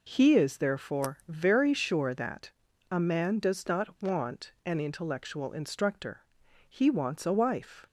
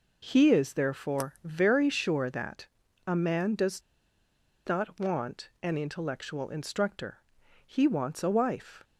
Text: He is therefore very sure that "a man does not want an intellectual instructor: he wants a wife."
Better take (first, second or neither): first